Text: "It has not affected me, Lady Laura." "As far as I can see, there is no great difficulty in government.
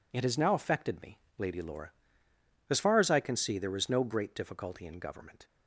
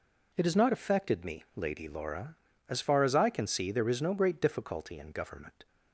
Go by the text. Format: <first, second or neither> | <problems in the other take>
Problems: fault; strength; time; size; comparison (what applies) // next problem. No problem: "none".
second | says "now" for "not"; at 0.3 s